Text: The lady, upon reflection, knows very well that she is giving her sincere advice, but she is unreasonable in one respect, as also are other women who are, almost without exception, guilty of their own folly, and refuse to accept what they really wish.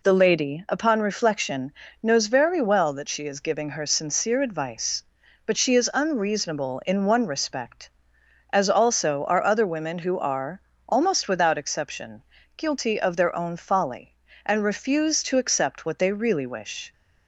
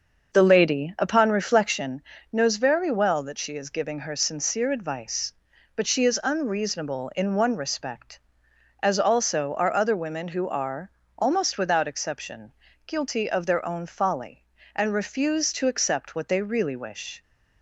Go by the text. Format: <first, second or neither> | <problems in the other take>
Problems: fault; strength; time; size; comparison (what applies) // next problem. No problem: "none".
first | starts louder than the rest; until 1.8 s; 6 dB